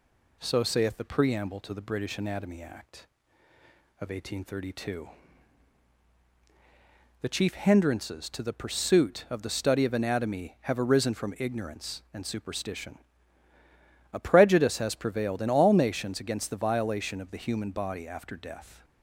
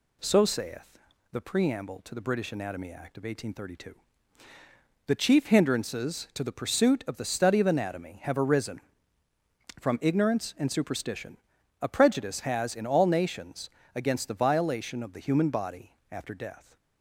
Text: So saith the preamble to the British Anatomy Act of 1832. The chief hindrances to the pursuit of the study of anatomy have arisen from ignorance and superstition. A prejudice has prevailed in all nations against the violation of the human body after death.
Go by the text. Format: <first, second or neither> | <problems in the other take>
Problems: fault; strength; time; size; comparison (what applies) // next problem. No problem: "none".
first | pauses between "saith" and "the"; noticeable; at 0.8 s; 0.48 s long // skips "prevailed"; at 12.7 s // pauses between "nations" and "against"; slight; at 13.6 s; 0.26 s long // pauses between "body" and "after"; slight; at 15.9 s; 0.20 s long